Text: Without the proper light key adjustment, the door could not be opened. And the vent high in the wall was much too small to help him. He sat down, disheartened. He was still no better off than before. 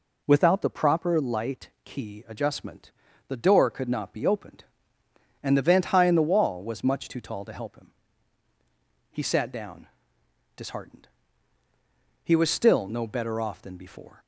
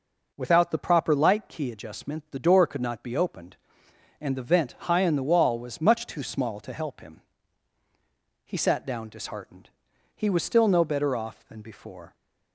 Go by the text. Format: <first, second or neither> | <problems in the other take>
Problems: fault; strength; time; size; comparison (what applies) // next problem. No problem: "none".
second | says "tall" for "small"; at 7.1 s